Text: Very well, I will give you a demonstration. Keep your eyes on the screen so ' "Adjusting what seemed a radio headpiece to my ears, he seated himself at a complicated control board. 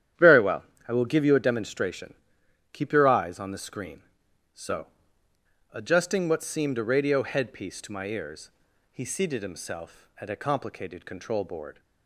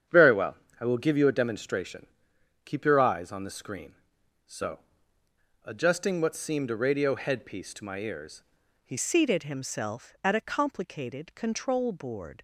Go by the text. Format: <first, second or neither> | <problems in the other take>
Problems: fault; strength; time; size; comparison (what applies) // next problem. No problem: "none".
first | starts louder than the rest; strong; until 1.3 s; 9 dB; strong in the first // changes voice at "seated"; from 8.9 s on; 3.5 s long